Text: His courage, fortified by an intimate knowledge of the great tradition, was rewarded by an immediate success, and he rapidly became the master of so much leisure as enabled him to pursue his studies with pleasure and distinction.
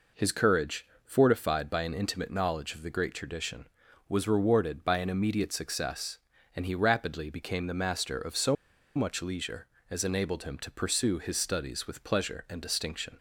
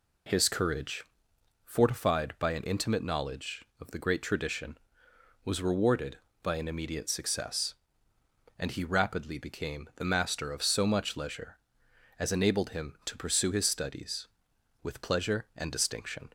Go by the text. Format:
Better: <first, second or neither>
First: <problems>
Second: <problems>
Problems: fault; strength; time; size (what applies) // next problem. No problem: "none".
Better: second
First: pauses between "so" and "much"; at 8.5 s; 0.41 s long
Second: none